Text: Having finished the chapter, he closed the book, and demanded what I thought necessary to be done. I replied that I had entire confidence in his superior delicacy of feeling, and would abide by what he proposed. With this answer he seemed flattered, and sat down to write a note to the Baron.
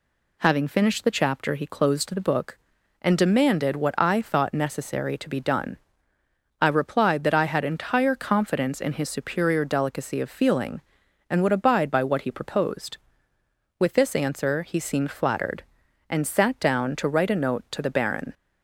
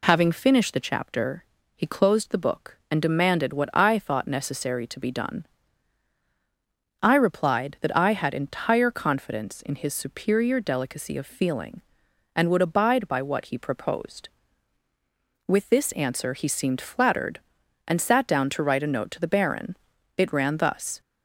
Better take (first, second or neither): first